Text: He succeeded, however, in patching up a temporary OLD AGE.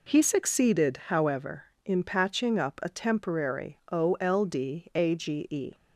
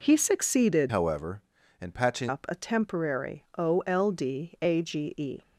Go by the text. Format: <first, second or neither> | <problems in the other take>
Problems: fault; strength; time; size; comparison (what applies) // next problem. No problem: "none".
first | changes voice from "however" to "patching"; from 0.8 to 2.2 s; 1.4 s long